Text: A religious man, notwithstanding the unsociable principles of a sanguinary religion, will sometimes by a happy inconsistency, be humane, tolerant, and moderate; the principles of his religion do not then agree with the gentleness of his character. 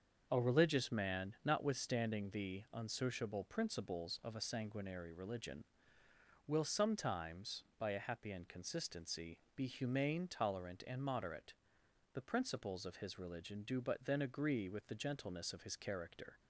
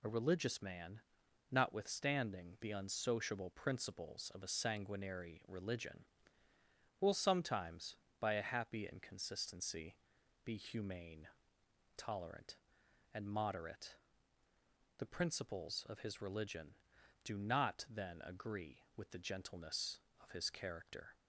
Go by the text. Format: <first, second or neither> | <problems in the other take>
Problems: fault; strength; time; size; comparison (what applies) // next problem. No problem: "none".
second | starts louder than the rest; until 1.3 s; 6.5 dB // says "but" for "not"; at 13.7 s